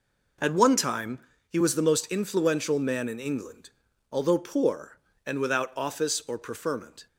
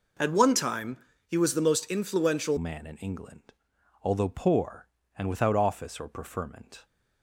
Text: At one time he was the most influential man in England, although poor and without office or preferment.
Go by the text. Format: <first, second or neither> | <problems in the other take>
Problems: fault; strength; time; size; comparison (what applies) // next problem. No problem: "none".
first | pauses between "time" and "he"; slight; at 0.9 s; 0.30 s long; slight in the first // changes voice at "man"; from 2.5 s on; 4.3 s long